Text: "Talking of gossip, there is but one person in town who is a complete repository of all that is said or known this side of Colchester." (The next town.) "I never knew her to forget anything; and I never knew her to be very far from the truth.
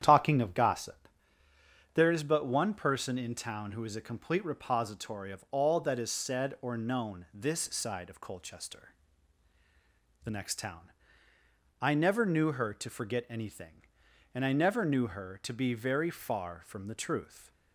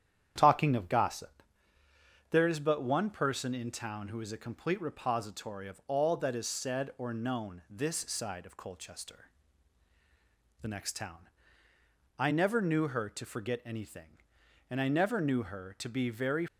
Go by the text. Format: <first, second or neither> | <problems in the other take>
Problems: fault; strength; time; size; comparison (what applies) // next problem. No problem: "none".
first | starts louder than the rest; strong; until 1.3 s; 9.5 dB; strong in the first // stops before "far from the truth"; at 16.4 s